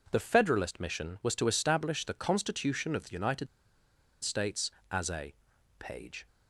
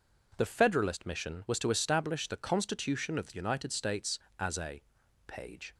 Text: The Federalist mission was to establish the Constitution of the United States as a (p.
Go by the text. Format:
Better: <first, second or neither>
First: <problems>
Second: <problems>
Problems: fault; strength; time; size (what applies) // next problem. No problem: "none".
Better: second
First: pauses between "United" and "States"; noticeable; at 3.4 s; 0.76 s long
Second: none